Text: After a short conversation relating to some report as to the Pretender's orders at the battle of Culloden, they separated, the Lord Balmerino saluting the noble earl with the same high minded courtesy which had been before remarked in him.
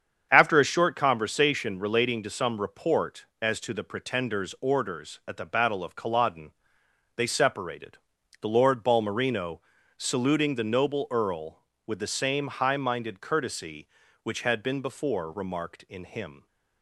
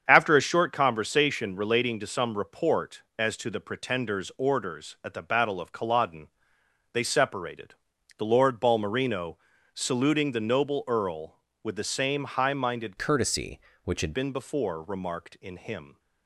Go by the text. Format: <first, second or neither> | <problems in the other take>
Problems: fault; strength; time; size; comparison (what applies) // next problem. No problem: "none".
first | starts louder than the rest; strong; until 1.0 s; 7.5 dB; strong in the first // pauses between "Balmerino" and "saluting"; at 9.3 s; 0.38 s long; also in the first // changes voice from "courtesy" to "had"; from 12.9 to 14.1 s; 1.2 s long